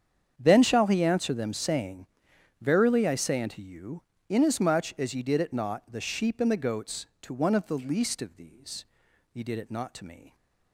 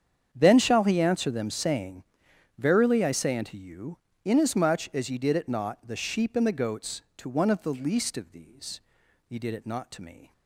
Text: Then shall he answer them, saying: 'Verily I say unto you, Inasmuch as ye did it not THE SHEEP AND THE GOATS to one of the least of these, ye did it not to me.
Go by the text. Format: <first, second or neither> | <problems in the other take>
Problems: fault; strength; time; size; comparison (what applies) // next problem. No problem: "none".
neither | starts louder than the rest; strong; the same in both